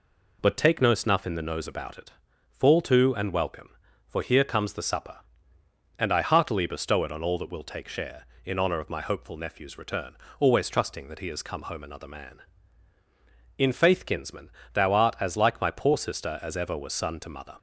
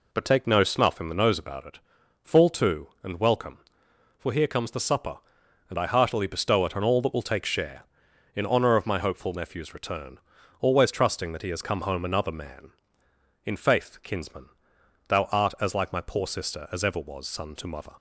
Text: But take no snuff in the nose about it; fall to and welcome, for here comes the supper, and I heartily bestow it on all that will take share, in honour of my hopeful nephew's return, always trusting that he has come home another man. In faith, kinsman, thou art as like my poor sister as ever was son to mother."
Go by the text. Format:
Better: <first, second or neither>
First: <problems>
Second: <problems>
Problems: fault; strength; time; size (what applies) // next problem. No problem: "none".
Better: neither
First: none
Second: none